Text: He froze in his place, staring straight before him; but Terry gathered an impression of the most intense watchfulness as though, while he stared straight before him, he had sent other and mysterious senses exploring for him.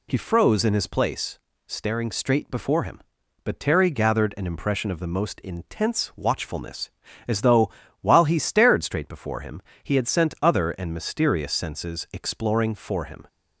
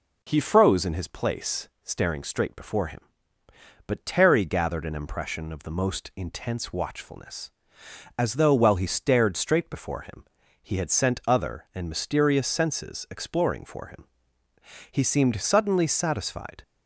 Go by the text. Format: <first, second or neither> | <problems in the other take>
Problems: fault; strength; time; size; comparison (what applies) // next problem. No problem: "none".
first | goes on to say "He seemed suddenly satisfied"; strong; from 14.9 s on; 1.7 s long